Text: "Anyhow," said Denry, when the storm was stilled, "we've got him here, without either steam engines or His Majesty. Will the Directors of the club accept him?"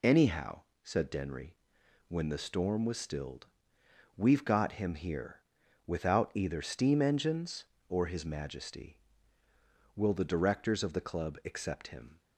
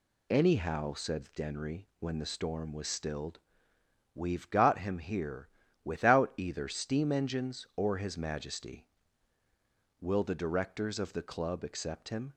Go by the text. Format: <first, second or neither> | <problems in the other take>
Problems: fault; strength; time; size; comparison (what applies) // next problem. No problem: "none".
neither | none